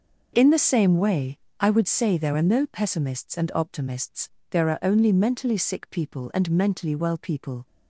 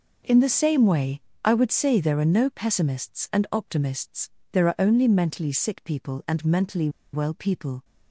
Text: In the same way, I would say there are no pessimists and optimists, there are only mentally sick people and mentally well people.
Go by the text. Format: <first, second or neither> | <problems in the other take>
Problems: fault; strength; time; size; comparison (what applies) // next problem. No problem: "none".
first | pauses between "mentally" and "well"; slight; at 6.8 s; 0.24 s long